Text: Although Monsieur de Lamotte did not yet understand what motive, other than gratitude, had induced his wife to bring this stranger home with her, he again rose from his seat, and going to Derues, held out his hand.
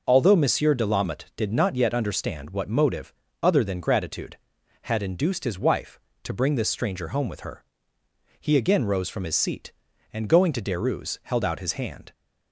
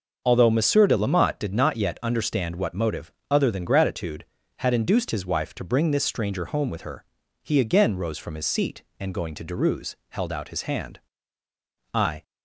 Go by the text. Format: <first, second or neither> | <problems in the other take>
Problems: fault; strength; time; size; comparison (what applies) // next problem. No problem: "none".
first | starts louder than the rest; until 1.2 s; 6 dB // goes on to say "I"; slight; from 11.9 s on; 0.30 s long